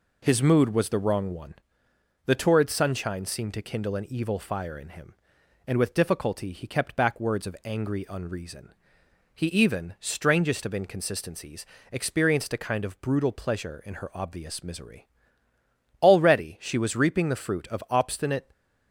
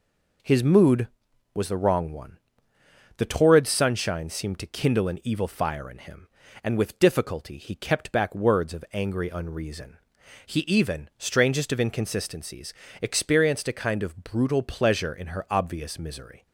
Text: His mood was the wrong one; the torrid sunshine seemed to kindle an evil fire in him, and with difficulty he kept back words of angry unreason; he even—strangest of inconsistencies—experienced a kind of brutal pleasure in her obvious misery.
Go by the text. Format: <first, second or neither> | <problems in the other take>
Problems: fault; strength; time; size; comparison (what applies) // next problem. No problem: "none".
second | goes on to say "Already she was reaping the fruit of obstinate"; strong; from 16.0 s on; 2.4 s long